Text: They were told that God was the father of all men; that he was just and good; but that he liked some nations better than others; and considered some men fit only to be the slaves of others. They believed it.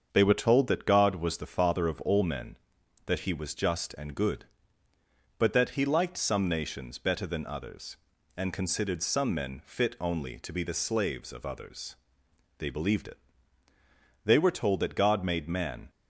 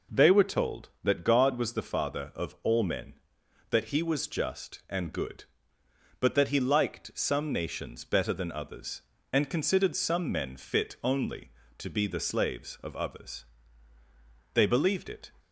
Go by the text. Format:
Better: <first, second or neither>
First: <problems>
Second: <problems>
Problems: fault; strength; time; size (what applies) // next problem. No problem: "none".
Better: second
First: starts louder than the rest; until 1.1 s; 7 dB // goes on to say "They were told that God made man"; from 14.2 s on; 1.6 s long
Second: none